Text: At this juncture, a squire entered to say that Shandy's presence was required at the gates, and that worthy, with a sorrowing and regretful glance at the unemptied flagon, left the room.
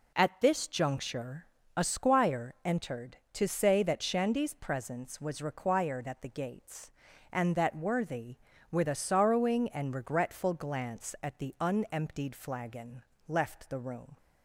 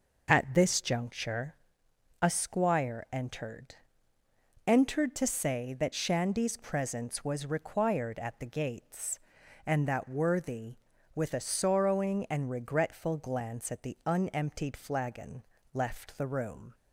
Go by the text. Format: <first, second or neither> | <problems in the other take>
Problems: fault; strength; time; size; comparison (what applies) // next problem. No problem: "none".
first | says "entered" twice; at 4.6 s